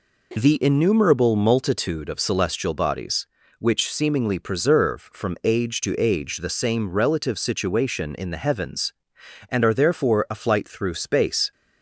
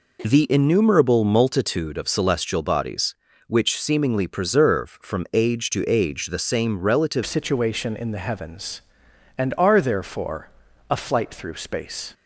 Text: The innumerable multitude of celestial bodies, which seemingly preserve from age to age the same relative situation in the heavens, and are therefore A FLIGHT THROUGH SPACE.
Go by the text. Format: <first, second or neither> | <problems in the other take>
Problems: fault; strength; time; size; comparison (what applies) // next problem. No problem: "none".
first | changes voice at "situation"; from 7.2 s on; 4.9 s long // pauses between "therefore" and "A"; at 10.4 s; 0.42 s long